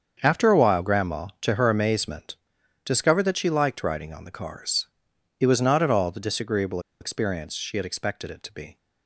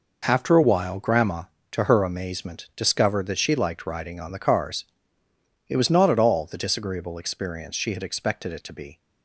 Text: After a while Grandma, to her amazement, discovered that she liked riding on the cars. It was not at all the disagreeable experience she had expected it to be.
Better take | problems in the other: second | starts louder than the rest; until 1.2 s; 7 dB // pauses between "disagreeable" and "experience"; slight; at 6.8 s; 0.20 s long

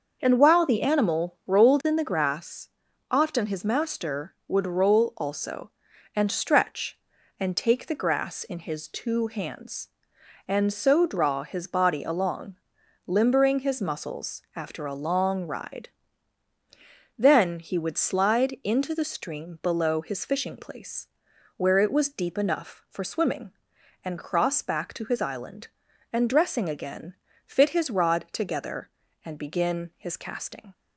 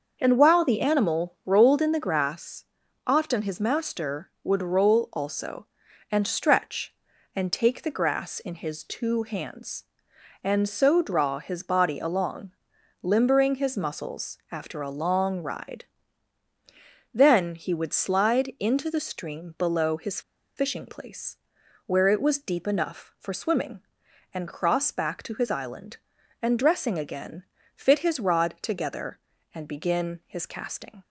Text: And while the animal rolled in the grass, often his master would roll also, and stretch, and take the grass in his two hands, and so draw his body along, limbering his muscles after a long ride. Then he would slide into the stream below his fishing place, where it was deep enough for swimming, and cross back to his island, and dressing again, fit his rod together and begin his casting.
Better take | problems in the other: first | starts louder than the rest; until 1.2 s; 6.5 dB; also in the first // pauses between "his" and "fishing"; at 20.1 s; 0.36 s long

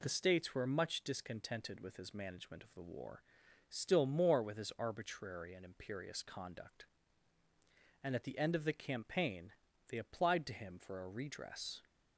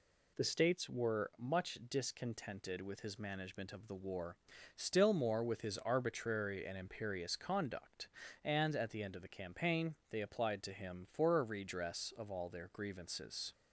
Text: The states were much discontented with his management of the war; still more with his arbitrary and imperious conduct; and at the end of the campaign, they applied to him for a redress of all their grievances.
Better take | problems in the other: second | stops before "of all their grievances"; at 11.8 s

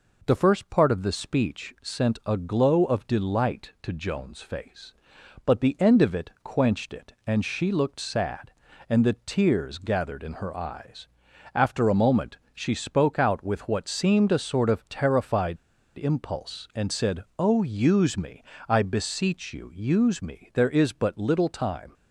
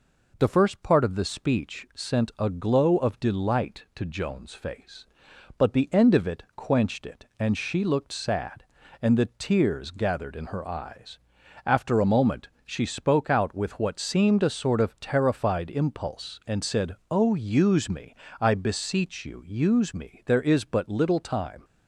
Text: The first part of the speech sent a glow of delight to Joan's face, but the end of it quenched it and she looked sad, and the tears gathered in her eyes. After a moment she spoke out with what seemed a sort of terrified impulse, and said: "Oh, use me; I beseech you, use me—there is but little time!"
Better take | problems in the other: second | pauses between "moment" and "she"; slight; at 12.3 s; 0.18 s long; slight in the second // pauses between "terrified" and "impulse"; at 15.5 s; 0.40 s long

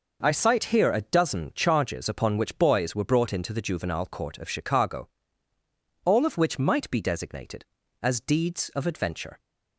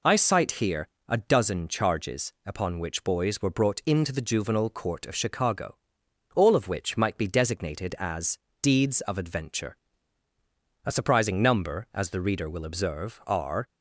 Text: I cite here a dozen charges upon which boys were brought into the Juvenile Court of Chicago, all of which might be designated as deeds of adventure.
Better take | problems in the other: first | pauses between "here" and "a"; slight; at 0.8 s; 0.18 s long // pauses between "as" and "deeds"; slight; at 8.3 s; 0.26 s long // goes on to say "A surprising number as the reader will observe are"; strong; from 10.8 s on; 2.8 s long

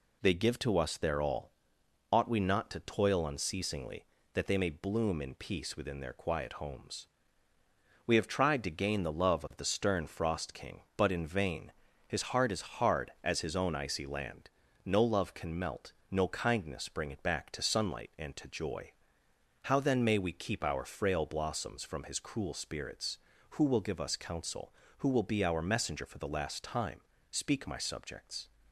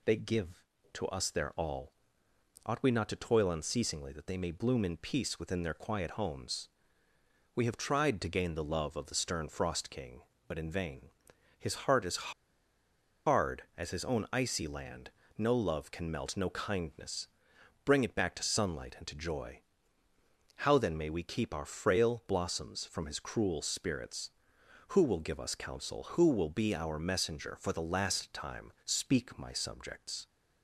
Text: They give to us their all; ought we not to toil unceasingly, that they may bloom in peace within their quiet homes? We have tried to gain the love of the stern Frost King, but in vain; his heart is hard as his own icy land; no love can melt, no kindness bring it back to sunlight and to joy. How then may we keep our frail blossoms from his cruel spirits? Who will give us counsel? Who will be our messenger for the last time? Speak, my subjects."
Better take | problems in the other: first | pauses between "is" and "hard"; noticeable; at 12.3 s; 0.95 s long // pauses between "kindness" and "bring"; noticeable; at 17.2 s; 0.56 s long

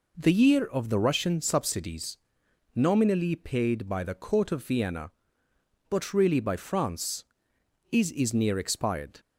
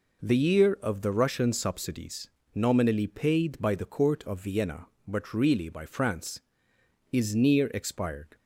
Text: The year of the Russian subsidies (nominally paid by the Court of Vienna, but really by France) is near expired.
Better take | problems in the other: second | says "is" twice; at 8.1 s

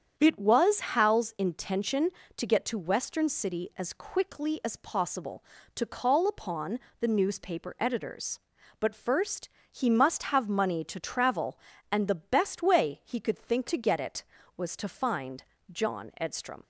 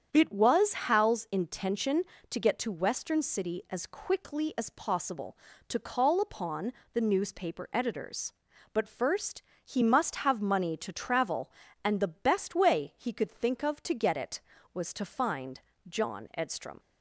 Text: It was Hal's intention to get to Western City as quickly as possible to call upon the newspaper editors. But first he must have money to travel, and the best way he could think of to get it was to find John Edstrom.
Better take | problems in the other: second | starts louder than the rest; strong; until 1.1 s; 8 dB; strong in the second // pauses between "upon" and "the"; slight; at 6.7 s; 0.22 s long; slight in the second // pauses between "first" and "he"; slight; at 9.4 s; 0.22 s long; slight in the second // skips "of"; at 13.6 s // pauses between "find" and "John"; slight; at 15.4 s; 0.28 s long; slight in the second

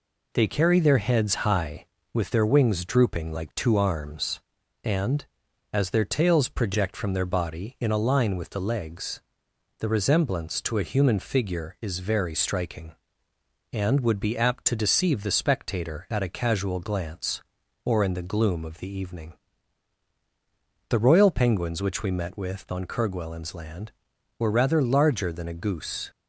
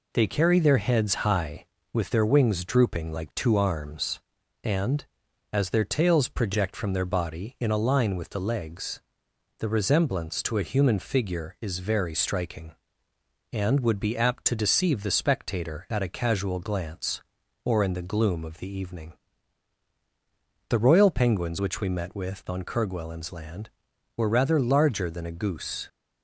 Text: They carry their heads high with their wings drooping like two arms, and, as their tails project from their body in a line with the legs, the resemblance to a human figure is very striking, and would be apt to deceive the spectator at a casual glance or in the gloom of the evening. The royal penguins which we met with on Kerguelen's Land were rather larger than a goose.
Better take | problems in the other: neither | none

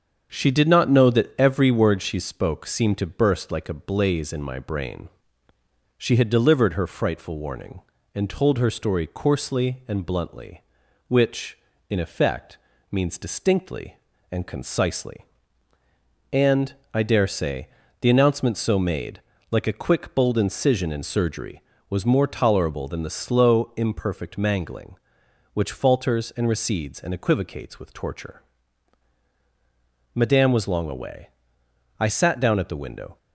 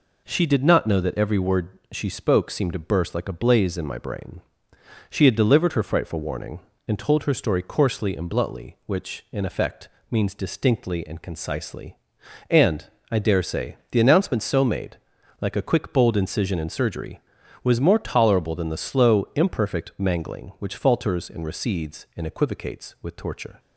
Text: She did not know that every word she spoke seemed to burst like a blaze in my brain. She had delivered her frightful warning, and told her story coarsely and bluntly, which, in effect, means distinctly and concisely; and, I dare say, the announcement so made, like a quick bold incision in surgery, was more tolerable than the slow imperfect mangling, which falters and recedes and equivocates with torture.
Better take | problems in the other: second | starts louder than the rest; strong; until 1.3 s; 7 dB // goes on to say "Madame was long away I sat down at the window"; strong; from 30.1 s on; 3.0 s long

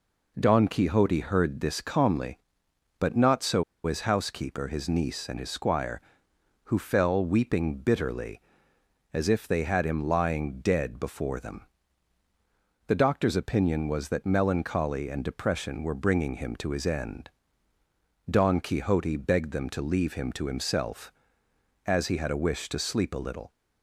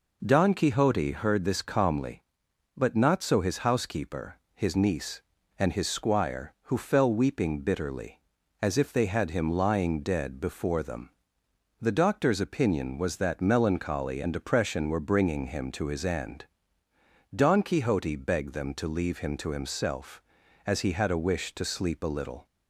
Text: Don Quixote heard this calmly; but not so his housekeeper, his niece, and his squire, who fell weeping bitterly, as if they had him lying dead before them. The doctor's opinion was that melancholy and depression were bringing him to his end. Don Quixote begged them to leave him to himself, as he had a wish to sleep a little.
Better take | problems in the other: second | pauses between "so" and "his"; slight; at 3.6 s; 0.23 s long

